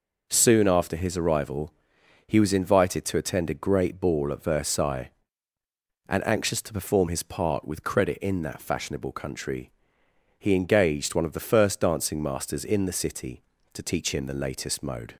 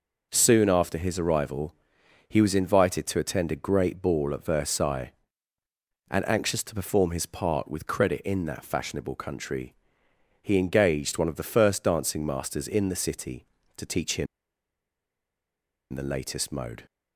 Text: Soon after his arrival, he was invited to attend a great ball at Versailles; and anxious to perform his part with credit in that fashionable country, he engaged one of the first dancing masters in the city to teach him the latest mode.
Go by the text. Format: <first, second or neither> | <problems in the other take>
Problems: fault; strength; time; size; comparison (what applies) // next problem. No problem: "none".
first | pauses between "him" and "the"; strong; at 14.2 s; 1.6 s long